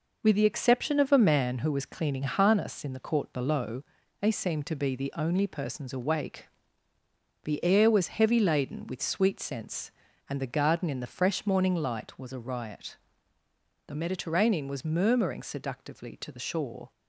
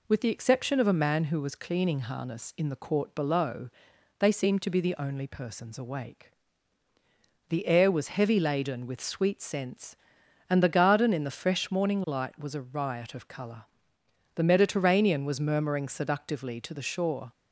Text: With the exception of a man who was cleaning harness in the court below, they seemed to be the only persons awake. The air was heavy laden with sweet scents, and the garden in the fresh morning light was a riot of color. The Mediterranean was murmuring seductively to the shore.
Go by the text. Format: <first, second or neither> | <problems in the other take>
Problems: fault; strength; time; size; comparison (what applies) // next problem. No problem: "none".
second | skips "of color"; at 13.4 s